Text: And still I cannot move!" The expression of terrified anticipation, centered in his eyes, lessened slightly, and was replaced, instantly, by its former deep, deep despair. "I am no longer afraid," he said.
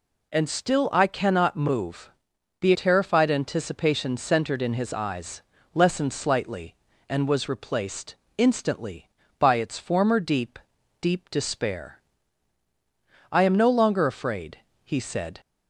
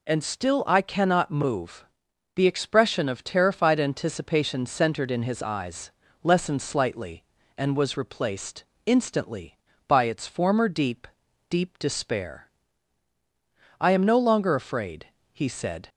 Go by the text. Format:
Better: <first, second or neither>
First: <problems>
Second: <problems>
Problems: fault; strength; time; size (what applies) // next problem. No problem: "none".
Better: second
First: skips "expression of"; at 2.7 s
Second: none